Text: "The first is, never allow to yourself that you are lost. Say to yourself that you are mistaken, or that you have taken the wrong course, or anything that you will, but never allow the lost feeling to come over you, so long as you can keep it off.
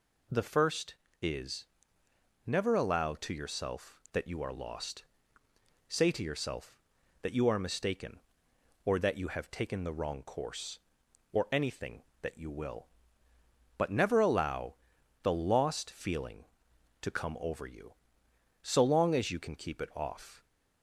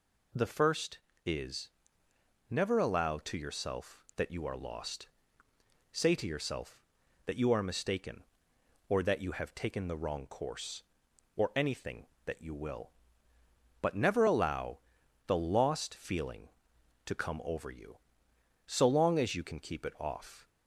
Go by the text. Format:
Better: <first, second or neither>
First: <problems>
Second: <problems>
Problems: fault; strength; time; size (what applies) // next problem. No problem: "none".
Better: neither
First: pauses between "allow" and "the"; noticeable; at 14.7 s; 0.48 s long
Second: pauses between "allow" and "the"; noticeable; at 14.7 s; 0.48 s long